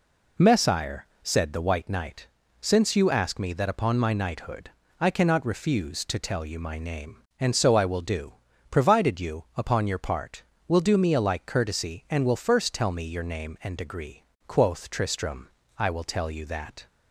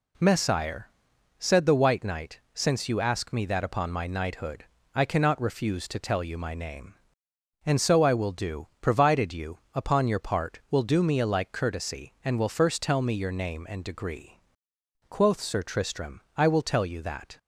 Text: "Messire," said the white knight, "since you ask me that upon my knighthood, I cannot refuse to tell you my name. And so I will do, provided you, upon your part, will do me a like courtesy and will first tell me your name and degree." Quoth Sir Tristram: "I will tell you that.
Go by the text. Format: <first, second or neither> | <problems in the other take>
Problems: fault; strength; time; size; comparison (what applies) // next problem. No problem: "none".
second | skips "Sir"; at 14.9 s